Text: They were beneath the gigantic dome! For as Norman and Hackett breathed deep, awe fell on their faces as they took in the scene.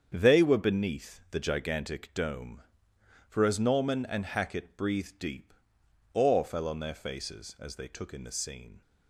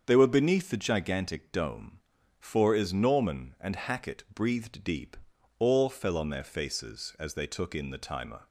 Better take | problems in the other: first | starts louder than the rest; until 1.0 s; 7 dB; strong in the first // says "timer" for "scene"; at 7.9 s

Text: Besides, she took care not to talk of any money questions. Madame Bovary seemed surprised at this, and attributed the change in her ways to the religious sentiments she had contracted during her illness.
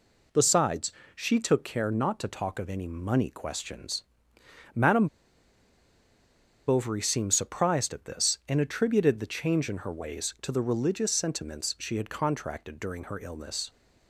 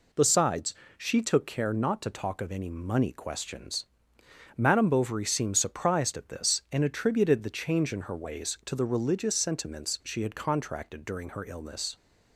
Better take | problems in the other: second | pauses between "Madame" and "Bovary"; strong; at 5.0 s; 1.5 s long

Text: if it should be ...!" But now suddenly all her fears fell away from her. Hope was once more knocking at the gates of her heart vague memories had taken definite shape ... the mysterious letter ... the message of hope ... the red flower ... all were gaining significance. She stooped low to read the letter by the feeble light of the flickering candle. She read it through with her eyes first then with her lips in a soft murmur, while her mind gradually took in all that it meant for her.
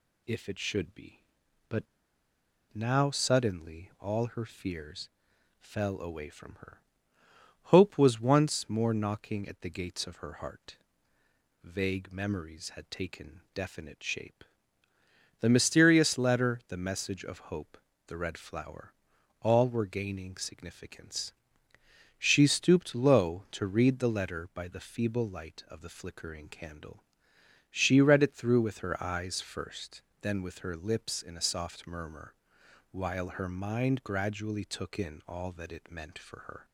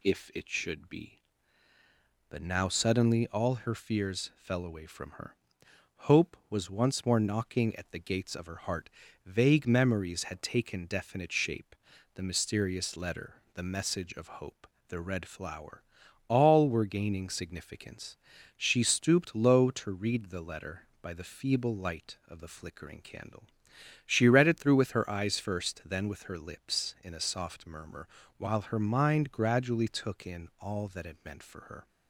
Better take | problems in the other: second | pauses between "But" and "now"; noticeable; at 1.8 s; 0.89 s long // pauses between "fears" and "fell"; noticeable; at 5.0 s; 0.50 s long // pauses between "heart" and "vague"; noticeable; at 10.7 s; 0.86 s long; also in the second // pauses between "first" and "then"; slight; at 30.0 s; 0.18 s long

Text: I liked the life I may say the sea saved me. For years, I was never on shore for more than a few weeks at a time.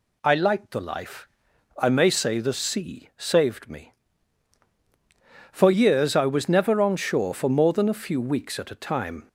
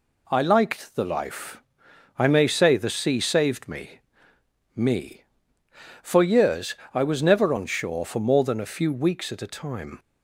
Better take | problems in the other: first | pauses between "life" and "I"; noticeable; at 1.6 s; 0.56 s long; noticeable in the first // says "me" twice; at 4.7 s

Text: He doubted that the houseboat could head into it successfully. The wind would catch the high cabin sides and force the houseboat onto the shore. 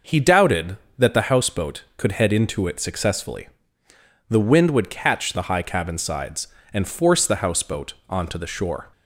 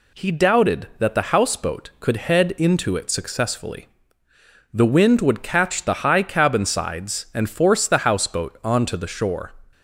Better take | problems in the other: neither | none

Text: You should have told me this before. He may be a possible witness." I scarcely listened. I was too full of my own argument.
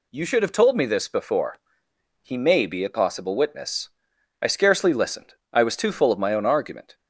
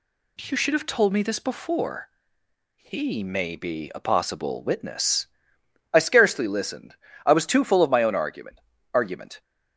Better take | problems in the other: first | says "argument" twice; at 8.9 s

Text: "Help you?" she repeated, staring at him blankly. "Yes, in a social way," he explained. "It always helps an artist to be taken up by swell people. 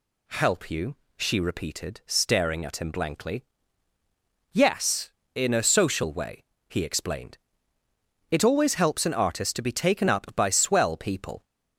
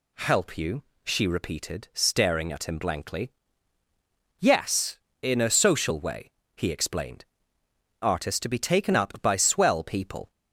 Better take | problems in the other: first | skips "It always helps an"; at 7.6 s

